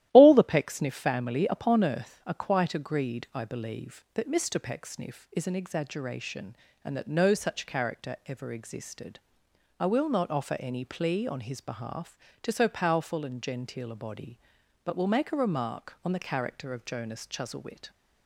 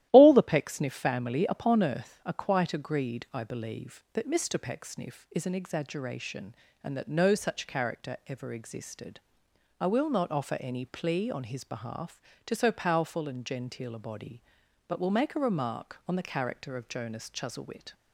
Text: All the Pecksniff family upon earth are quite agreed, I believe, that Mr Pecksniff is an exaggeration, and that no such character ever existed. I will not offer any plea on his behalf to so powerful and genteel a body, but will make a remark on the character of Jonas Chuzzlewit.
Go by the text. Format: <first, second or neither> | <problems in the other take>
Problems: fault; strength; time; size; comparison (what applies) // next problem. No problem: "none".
neither | starts louder than the rest; strong; the same in both